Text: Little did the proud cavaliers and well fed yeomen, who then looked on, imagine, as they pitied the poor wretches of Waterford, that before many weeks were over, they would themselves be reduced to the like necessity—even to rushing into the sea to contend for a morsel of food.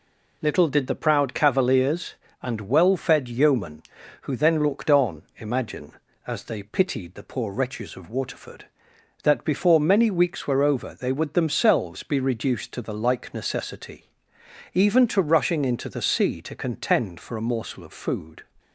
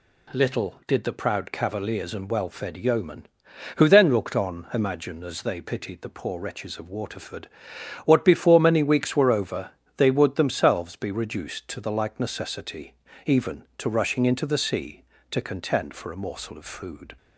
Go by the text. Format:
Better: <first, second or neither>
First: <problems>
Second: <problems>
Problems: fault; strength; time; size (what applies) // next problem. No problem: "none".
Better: first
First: none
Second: says "what" for "that"; at 8.0 s